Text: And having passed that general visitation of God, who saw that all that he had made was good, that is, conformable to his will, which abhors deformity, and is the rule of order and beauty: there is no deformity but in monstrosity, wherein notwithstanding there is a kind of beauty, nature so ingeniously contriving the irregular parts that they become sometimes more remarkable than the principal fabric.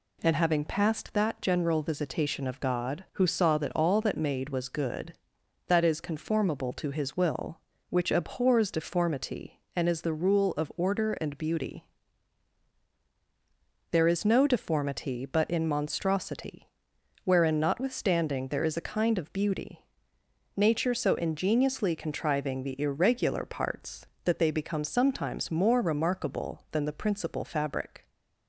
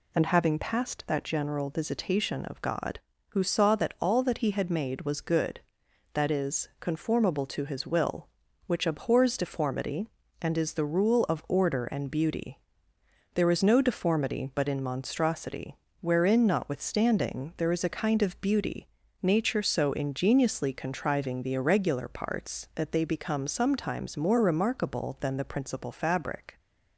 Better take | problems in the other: second | skips "he had"; at 4.1 s

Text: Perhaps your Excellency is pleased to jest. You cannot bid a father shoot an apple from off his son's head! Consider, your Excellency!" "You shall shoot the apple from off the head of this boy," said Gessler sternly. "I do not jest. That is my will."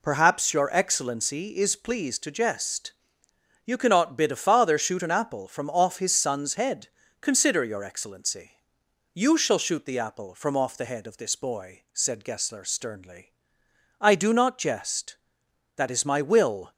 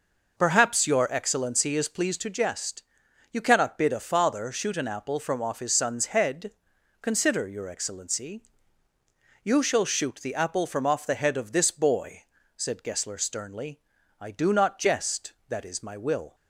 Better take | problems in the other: neither | none

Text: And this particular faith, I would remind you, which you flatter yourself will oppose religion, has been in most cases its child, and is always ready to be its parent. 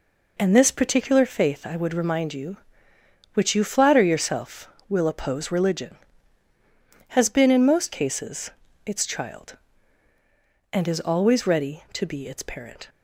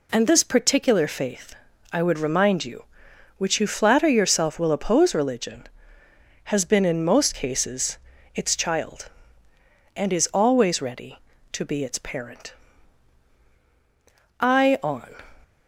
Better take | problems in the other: first | pauses between "cases" and "its"; at 7.9 s; 0.38 s long; slight in the first // goes on to say "I on"; noticeable; from 14.4 s on; 0.90 s long

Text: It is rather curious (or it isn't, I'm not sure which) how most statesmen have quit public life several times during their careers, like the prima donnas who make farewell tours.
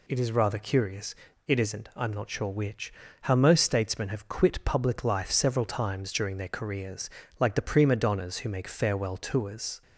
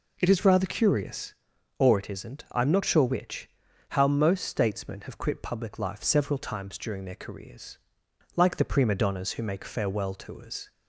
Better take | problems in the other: second | skips "or"; at 1.3 s

